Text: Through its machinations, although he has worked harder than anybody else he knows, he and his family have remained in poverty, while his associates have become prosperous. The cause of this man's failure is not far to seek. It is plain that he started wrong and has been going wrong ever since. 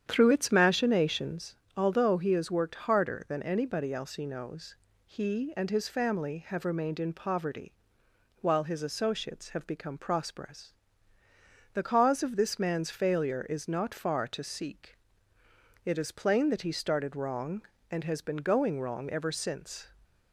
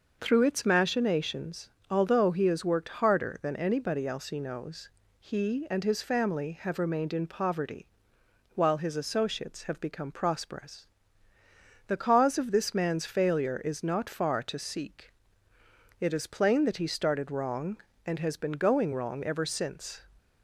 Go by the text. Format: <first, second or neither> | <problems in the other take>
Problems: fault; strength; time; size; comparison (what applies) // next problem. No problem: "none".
second | starts louder than the rest; strong; until 1.5 s; 9 dB